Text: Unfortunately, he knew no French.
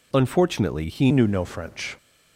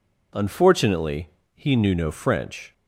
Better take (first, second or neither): second